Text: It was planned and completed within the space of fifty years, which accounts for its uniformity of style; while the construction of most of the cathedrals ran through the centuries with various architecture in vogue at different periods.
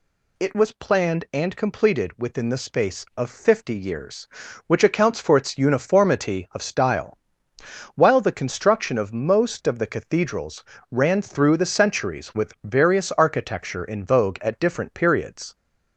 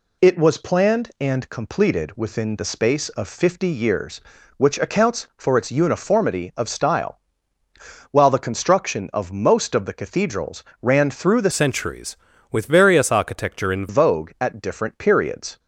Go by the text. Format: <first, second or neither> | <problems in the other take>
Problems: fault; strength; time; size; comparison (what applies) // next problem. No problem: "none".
first | pauses between "cathedrals" and "ran"; slight; at 10.6 s; 0.18 s long; slight in the first // changes voice from "centuries" to "in"; from 11.5 to 13.8 s; 2.3 s long